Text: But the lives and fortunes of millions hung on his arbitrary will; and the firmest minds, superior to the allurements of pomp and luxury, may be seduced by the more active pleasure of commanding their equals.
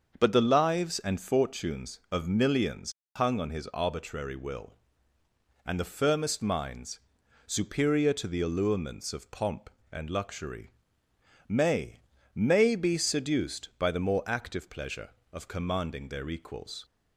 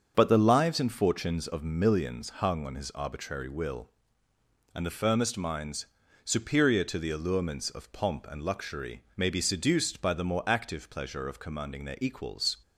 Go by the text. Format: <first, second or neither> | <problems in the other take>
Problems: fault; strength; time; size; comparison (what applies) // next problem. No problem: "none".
second | starts louder than the rest; until 1.1 s; 6.5 dB; also in the second // pauses between "millions" and "hung"; slight; at 2.9 s; 0.24 s long // says "may" twice; at 12.3 s